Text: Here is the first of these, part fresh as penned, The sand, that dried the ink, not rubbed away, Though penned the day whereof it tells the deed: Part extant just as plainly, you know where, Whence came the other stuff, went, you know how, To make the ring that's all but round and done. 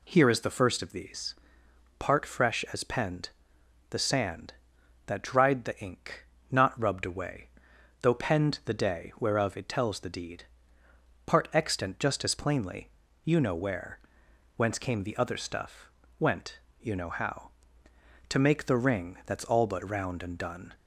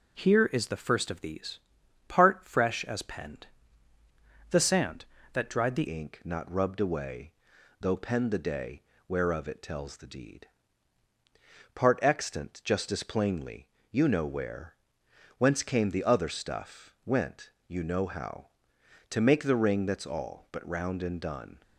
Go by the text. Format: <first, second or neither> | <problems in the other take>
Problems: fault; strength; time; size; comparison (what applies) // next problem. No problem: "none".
first | changes voice at "ink"; from 5.8 s on; 15.8 s long // pauses between "day" and "whereof"; slight; at 8.8 s; 0.24 s long